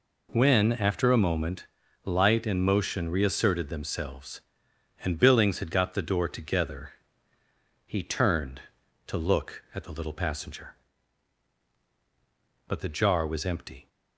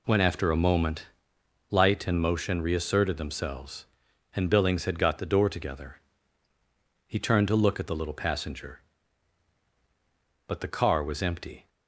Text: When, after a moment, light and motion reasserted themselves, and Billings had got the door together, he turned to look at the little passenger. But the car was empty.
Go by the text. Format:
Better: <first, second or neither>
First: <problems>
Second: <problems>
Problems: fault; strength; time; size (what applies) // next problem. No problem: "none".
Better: second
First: says "jar" for "car"; at 12.8 s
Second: none